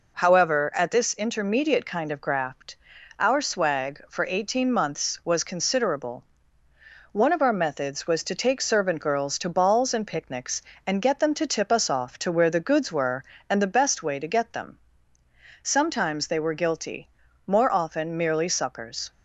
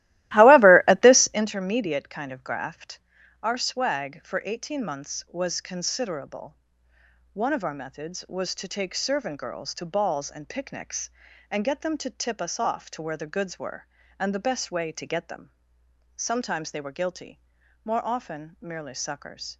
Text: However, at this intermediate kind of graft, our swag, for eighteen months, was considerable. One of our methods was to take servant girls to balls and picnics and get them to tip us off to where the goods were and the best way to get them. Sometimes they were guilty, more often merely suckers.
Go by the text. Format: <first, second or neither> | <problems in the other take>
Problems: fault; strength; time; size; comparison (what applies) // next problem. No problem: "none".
first | starts louder than the rest; strong; until 1.5 s; 17 dB